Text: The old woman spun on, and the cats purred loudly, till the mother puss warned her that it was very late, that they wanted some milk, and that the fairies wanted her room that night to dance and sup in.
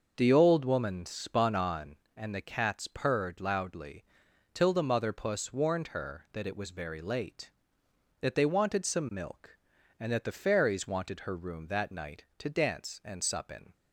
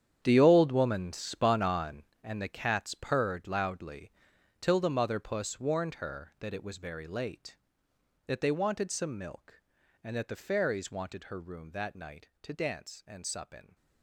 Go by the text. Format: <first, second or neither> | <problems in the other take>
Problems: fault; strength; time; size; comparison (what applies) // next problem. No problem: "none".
first | gets quieter; strong; throughout; 14 dB // starts louder than the rest; strong; until 1.2 s; 9 dB; noticeable in the first